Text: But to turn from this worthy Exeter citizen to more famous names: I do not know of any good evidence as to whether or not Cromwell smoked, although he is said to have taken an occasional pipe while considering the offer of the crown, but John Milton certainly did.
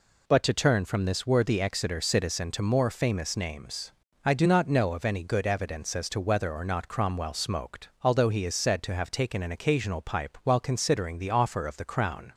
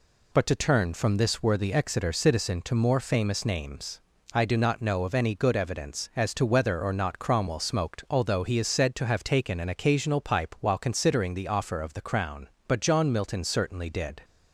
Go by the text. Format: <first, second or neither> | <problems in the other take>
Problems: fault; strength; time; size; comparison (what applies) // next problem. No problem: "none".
second | stops before "but John Milton certainly did"; at 12.3 s